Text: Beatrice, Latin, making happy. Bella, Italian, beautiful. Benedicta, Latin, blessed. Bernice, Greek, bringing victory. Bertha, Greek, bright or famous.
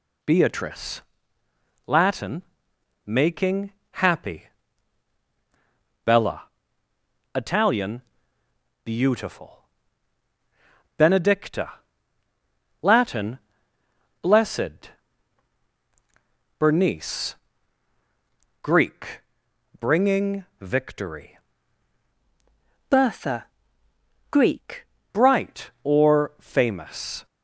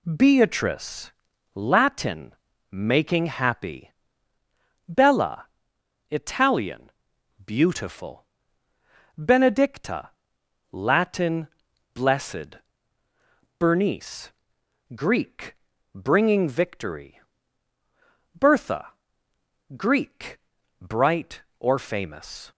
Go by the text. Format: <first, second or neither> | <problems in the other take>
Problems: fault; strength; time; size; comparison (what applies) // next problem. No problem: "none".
second | pauses between "making" and "happy"; slight; at 3.7 s; 0.20 s long // pauses between "bringing" and "victory"; slight; at 20.4 s; 0.16 s long // changes voice from "Bertha" to "Greek"; from 22.8 to 24.8 s; 2.0 s long